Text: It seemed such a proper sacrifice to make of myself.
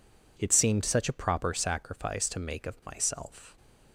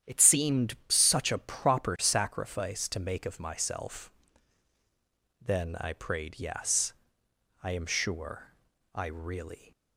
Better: first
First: none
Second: starts louder than the rest; strong; until 1.1 s; 9.5 dB // goes on to say "Then I prayed yes I am sure I really"; strong; from 5.4 s on; 4.3 s long

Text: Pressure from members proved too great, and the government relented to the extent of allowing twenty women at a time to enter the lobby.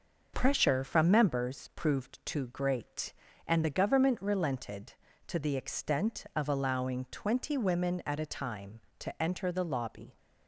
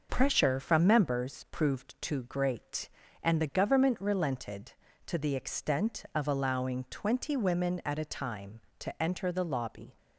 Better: neither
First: starts louder than the rest; until 1.3 s; 6 dB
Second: starts louder than the rest; until 1.1 s; 6.5 dB

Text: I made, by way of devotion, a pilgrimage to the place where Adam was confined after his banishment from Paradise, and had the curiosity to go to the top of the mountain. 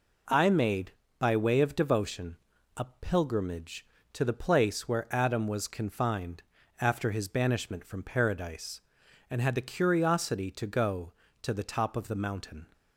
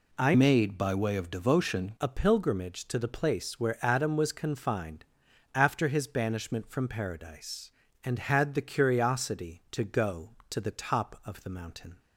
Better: first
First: pauses between "confined" and "after"; at 6.4 s; 0.40 s long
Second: changes voice from "made" to "devotion"; from 0.3 to 1.9 s; 1.6 s long // pauses between "confined" and "after"; noticeable; at 5.0 s; 0.52 s long

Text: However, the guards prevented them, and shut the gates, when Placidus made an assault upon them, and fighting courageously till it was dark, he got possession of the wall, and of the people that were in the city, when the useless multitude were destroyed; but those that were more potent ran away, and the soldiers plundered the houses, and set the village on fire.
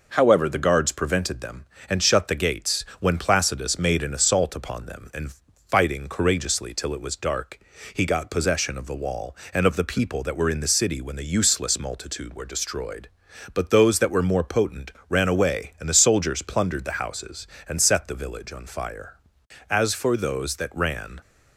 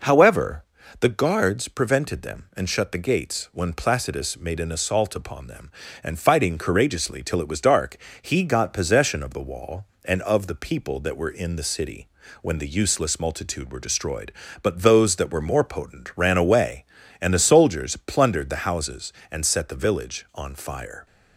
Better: second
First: pauses between "and" and "fighting"; slight; at 5.3 s; 0.36 s long // pauses between "potent" and "ran"; slight; at 14.9 s; 0.18 s long // goes on to say "As for those that ran"; from 19.6 s on; 1.5 s long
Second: none

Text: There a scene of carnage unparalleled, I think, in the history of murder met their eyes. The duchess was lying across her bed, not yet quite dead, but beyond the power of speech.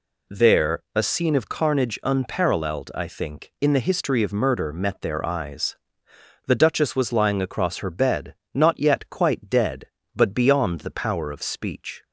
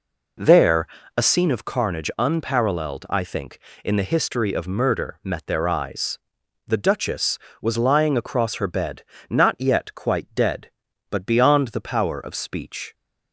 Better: first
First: none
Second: starts louder than the rest; noticeable; until 1.5 s; 4.5 dB // pauses between "There" and "a"; slight; at 0.8 s; 0.30 s long

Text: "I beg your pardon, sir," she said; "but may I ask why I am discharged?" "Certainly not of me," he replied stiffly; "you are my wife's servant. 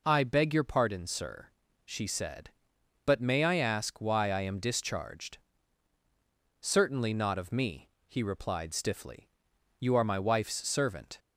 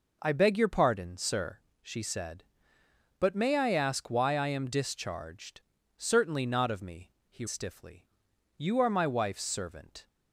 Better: first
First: none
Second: skips "replied"; at 7.4 s

